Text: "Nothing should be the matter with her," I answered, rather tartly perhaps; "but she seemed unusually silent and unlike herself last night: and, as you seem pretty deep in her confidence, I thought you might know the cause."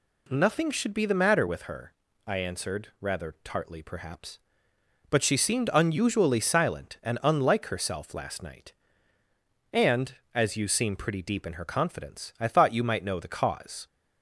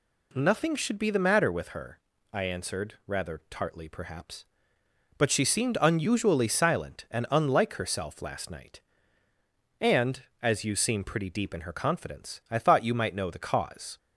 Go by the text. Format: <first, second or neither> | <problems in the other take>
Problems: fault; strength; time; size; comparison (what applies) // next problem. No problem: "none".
neither | none